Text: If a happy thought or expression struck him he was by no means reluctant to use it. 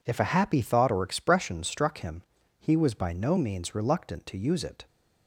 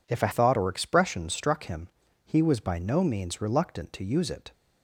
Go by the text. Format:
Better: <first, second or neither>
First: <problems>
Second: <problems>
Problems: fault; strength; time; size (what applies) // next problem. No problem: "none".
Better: first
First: pauses between "him" and "he"; slight; at 2.2 s; 0.34 s long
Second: skips "happy"; at 0.3 s // pauses between "him" and "he"; slight; at 1.8 s; 0.34 s long